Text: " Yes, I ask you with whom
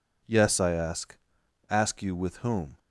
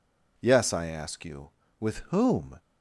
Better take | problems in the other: second | says "ask" twice; at 1.6 s

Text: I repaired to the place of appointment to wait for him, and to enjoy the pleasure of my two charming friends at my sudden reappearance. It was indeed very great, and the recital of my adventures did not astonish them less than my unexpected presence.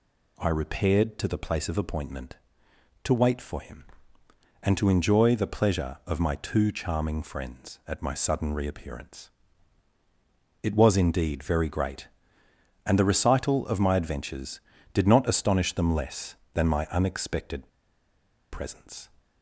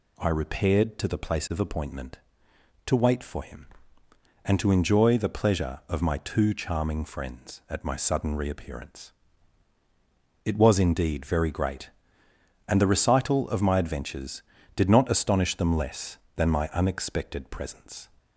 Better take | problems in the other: second | pauses between "unexpected" and "presence"; noticeable; at 17.6 s; 0.84 s long

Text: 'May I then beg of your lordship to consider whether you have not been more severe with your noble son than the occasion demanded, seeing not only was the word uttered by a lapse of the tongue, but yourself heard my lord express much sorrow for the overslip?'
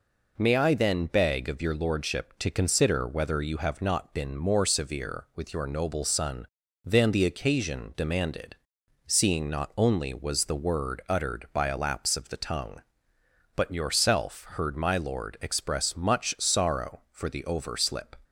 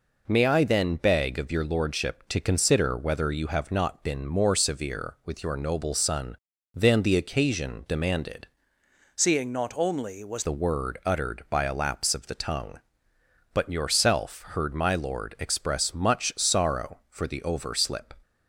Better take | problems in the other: first | changes voice from "seeing" to "was"; from 9.1 to 10.4 s; 1.3 s long

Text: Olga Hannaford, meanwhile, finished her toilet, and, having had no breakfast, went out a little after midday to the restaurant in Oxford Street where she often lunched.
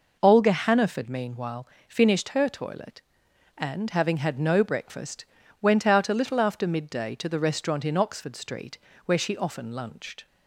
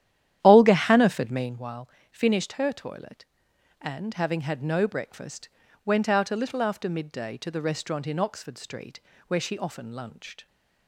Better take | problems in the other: first | starts louder than the rest; strong; until 1.6 s; 11.5 dB // pauses between "Street" and "where"; slight; at 9.0 s; 0.26 s long; slight in the first

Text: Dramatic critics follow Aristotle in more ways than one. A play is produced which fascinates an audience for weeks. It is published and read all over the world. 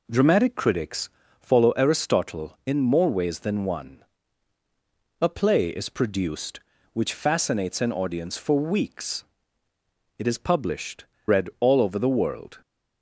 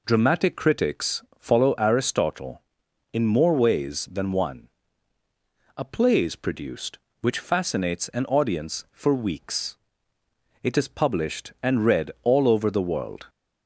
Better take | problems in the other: second | pauses between "critics" and "follow"; slight; at 1.0 s; 0.30 s long; slight in the second // skips "and"; at 11.1 s

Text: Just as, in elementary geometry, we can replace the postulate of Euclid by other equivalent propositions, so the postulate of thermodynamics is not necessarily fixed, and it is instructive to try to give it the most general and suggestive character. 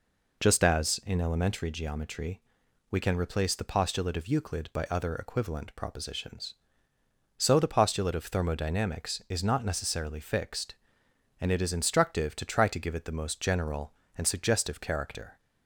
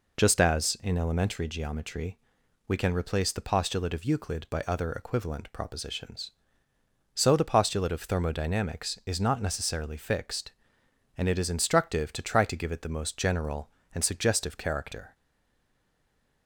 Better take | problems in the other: first | stays silent after the last word; noticeable; from 15.1 s on; 1.3 s long

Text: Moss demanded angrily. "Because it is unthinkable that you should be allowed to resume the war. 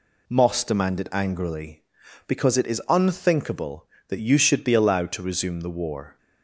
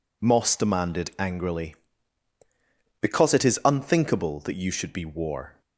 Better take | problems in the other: first | skips "allowed to resume the"; at 5.0 s

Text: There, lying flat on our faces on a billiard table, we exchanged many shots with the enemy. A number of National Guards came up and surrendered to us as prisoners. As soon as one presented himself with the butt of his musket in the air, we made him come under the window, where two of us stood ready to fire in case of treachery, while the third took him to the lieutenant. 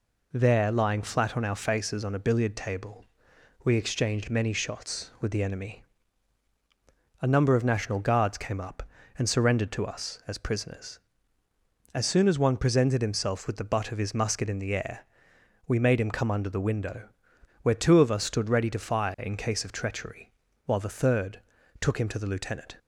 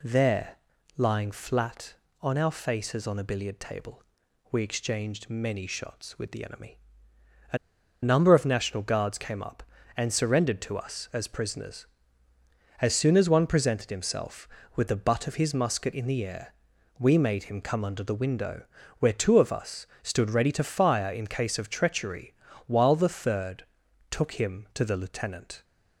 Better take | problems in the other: first | pauses between "A" and "number"; at 7.5 s; 0.45 s long // pauses between "us" and "stood"; slight; at 19.8 s; 0.16 s long // pauses between "third" and "took"; noticeable; at 23.6 s; 0.48 s long; also in the first

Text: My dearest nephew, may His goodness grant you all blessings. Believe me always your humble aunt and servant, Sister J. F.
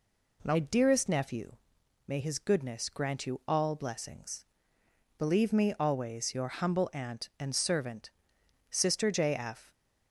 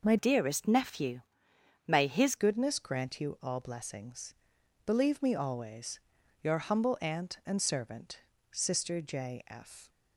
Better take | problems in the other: first | changes voice from "dearest" to "His"; from 0.1 to 2.3 s; 2.2 s long // pauses between "always" and "your"; noticeable; at 5.9 s; 0.46 s long

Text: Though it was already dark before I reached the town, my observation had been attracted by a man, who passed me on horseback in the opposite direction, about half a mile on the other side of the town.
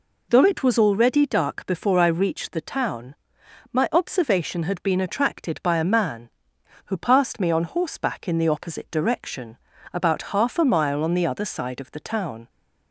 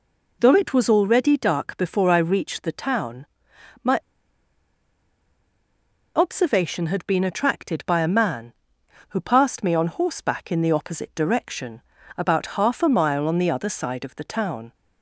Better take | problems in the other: first | pauses between "my" and "observation"; strong; at 3.9 s; 2.1 s long

